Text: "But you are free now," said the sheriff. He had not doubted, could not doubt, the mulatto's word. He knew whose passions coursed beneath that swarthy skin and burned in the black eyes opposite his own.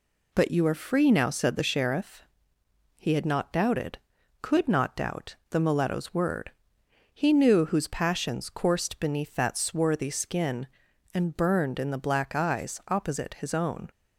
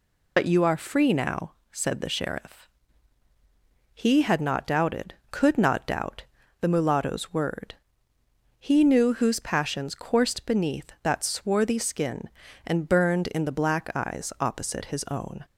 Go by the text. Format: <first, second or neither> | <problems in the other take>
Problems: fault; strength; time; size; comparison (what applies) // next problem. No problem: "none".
first | loses the start of "But"; at 0.3 s; 80 ms